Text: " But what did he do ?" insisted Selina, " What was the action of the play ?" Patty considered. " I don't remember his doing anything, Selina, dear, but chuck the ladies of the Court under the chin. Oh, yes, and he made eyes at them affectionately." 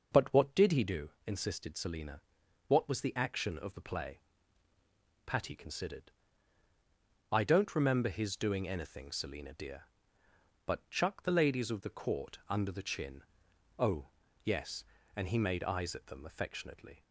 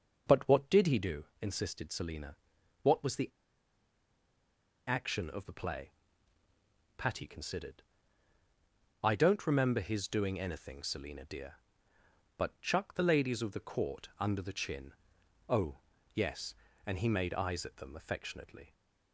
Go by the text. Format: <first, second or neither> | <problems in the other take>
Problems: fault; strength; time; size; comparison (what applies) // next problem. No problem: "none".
first | starts louder than the rest; strong; until 1.3 s; 7.5 dB; strong in the first // pauses between "the" and "action"; strong; at 3.2 s; 1.5 s long